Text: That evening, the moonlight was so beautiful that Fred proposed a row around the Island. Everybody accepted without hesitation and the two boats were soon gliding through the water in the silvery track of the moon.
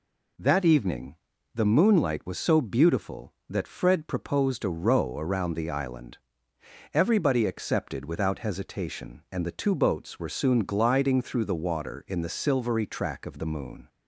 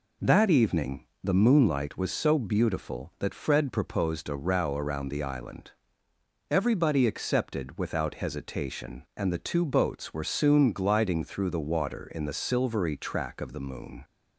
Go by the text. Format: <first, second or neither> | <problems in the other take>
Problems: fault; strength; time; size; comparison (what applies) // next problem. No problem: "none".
neither | none